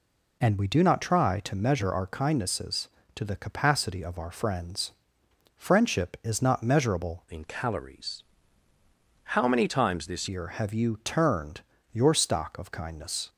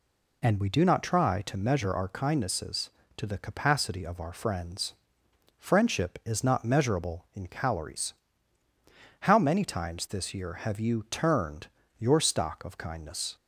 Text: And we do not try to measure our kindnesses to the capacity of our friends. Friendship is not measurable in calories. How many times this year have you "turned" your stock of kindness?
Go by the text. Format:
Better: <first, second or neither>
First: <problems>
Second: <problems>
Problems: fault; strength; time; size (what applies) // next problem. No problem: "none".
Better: second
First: changes voice from "in" to "this"; from 7.3 to 10.2 s; 2.9 s long // pauses between "turned" and "your"; slight; at 11.6 s; 0.30 s long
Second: pauses between "turned" and "your"; slight; at 11.6 s; 0.30 s long